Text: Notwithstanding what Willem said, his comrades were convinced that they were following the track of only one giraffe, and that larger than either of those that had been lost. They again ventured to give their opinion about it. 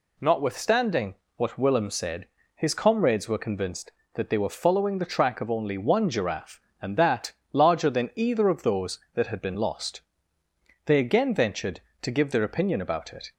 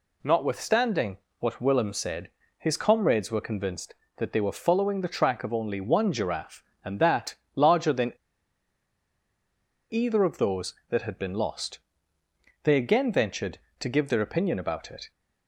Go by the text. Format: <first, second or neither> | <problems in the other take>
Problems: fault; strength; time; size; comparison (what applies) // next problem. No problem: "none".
first | pauses between "Notwithstanding" and "what"; slight; at 1.1 s; 0.22 s long; slight in the first // pauses between "that" and "larger"; slight; at 7.3 s; 0.22 s long; slight in the first // pauses between "than" and "either"; strong; at 8.1 s; 1.7 s long